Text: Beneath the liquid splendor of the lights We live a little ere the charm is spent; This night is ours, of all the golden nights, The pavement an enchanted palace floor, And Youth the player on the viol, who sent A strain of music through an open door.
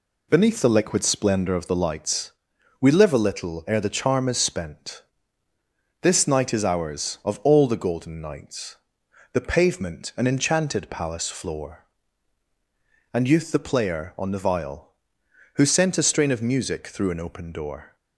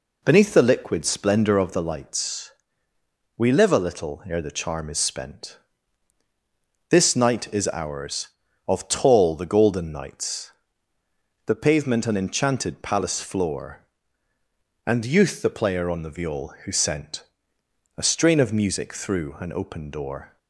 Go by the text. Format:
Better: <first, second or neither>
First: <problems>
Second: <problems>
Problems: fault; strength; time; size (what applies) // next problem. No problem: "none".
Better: first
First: pauses between "lights" and "We"; noticeable; at 2.2 s; 0.50 s long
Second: pauses between "lights" and "We"; noticeable; at 2.5 s; 0.84 s long // says "tall" for "all"; at 8.8 s // pauses between "sent" and "A"; noticeable; at 17.2 s; 0.74 s long